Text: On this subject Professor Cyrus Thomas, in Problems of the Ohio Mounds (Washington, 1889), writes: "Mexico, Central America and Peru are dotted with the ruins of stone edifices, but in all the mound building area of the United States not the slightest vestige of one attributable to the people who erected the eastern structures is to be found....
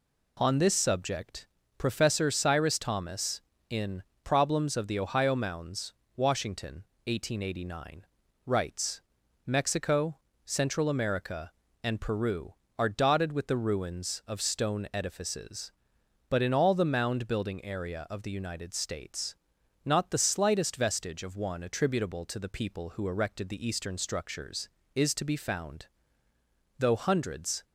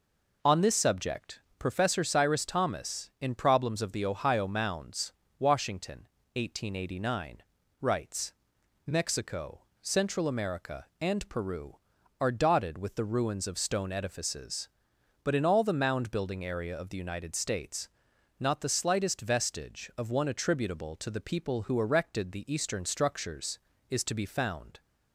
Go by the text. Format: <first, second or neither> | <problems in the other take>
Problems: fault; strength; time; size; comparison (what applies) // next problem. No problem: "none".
second | pauses between "subject" and "Professor"; slight; at 1.4 s; 0.30 s long; slight in the second // pauses between "in" and "Problems"; slight; at 4.0 s; 0.18 s long // pauses between "States" and "not"; noticeable; at 19.3 s; 0.50 s long; noticeable in the second // goes on to say "Though hundreds"; noticeable; from 26.7 s on; 0.86 s long